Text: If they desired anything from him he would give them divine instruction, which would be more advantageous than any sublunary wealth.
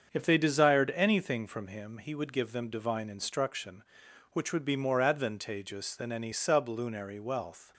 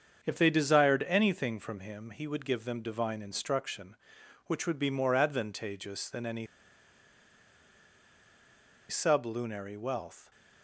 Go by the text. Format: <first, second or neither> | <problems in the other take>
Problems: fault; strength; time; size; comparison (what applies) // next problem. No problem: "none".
first | starts louder than the rest; strong; until 1.2 s; 7 dB; strong in the first // pauses between "any" and "sublunary"; strong; at 6.4 s; 2.4 s long